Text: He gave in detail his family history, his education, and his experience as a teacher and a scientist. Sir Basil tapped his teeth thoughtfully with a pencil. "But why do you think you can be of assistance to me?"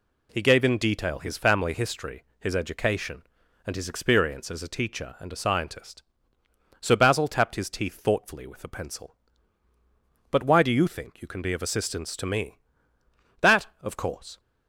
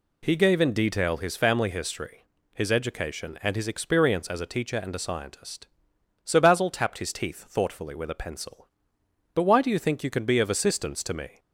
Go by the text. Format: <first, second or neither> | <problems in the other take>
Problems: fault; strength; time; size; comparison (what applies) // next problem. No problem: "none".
second | goes on to say "That of course"; noticeable; from 13.3 s on; 1.0 s long